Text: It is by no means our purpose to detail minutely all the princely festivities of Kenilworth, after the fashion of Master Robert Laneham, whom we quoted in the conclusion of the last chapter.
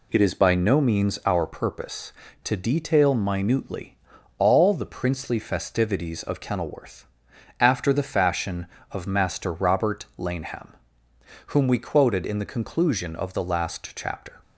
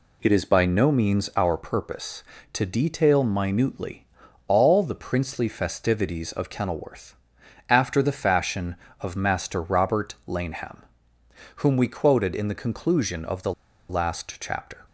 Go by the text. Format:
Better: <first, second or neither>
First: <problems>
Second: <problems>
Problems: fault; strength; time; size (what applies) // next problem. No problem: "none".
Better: first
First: pauses between "minutely" and "all"; at 3.9 s; 0.42 s long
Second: pauses between "minutely" and "all"; at 4.0 s; 0.42 s long // pauses between "the" and "last"; at 13.5 s; 0.36 s long